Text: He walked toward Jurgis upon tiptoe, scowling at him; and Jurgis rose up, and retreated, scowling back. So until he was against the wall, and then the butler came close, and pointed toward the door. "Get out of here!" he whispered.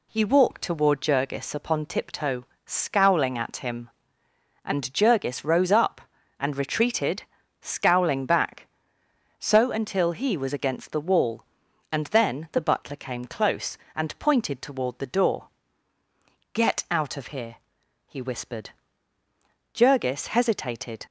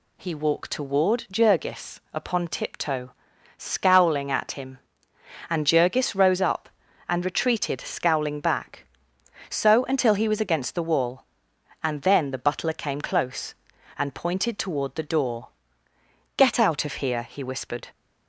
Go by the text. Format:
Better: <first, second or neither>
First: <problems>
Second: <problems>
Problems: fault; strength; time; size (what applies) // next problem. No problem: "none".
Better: second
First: goes on to say "Jurgis hesitated"; noticeable; from 19.7 s on; 1.3 s long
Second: none